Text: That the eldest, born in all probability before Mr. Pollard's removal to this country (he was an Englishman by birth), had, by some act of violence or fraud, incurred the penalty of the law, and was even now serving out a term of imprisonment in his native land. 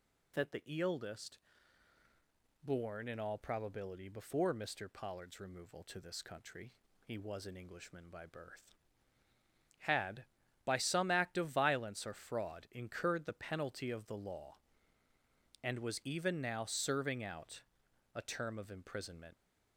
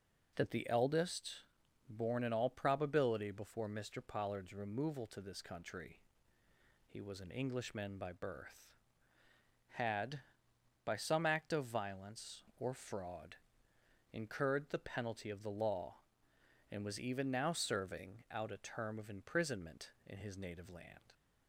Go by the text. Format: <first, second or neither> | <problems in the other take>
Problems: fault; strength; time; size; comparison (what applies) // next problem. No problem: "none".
second | pauses between "the" and "eldest"; slight; at 0.6 s; 0.20 s long // pauses between "out" and "a"; noticeable; at 17.6 s; 0.54 s long // stops before "in his native land"; at 19.3 s